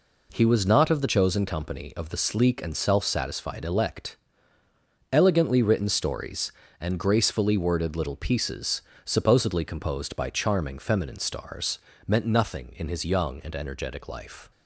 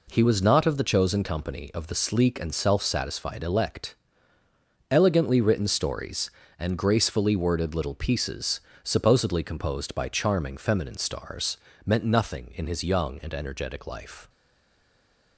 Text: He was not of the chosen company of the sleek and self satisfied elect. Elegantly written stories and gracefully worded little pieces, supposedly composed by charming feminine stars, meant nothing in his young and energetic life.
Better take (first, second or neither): first